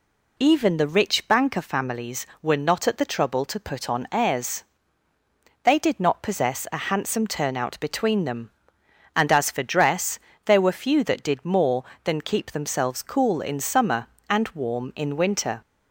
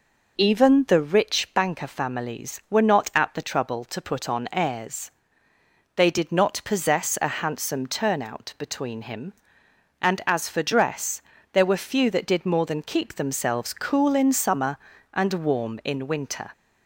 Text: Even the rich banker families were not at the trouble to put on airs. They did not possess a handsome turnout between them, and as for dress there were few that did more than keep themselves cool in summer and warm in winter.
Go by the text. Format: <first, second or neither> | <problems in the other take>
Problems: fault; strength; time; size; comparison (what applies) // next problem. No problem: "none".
first | says "him" for "them"; at 9.0 s // pauses between "dress" and "there"; slight; at 11.2 s; 0.30 s long; slight in the first